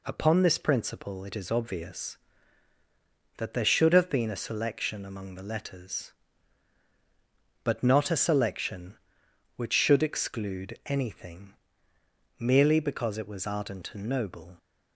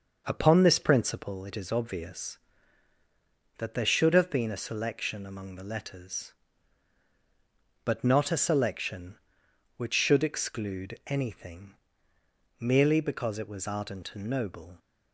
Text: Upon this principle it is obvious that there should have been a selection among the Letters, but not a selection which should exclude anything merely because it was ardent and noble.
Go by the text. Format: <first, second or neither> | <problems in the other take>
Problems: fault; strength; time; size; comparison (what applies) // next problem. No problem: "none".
first | starts louder than the rest; until 1.4 s; 6.5 dB // pauses between "anything" and "merely"; noticeable; at 11.7 s; 0.86 s long; noticeable in the first